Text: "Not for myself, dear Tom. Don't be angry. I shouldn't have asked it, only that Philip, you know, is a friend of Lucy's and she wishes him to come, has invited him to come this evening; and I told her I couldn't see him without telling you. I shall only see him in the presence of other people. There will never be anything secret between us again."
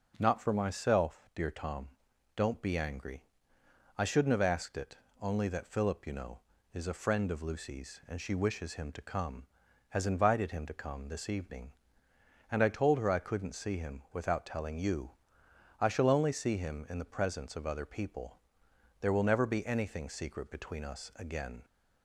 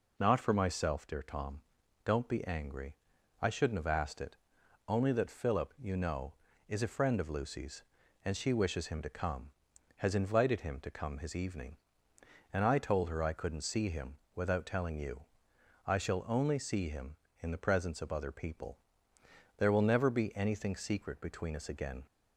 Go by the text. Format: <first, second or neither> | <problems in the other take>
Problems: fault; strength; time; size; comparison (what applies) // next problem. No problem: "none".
first | says "his" for "this"; at 11.1 s // pauses between "him" and "without"; slight; at 14.1 s; 0.18 s long